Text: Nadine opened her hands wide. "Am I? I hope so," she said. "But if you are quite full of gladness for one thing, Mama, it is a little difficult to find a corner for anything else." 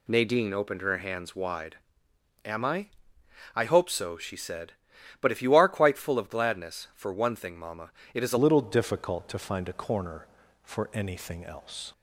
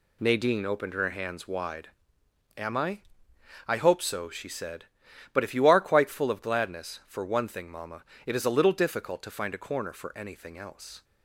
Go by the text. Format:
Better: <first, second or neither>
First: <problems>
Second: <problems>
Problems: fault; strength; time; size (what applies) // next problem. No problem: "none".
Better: second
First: changes voice at "little"; from 8.3 s on; 3.6 s long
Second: none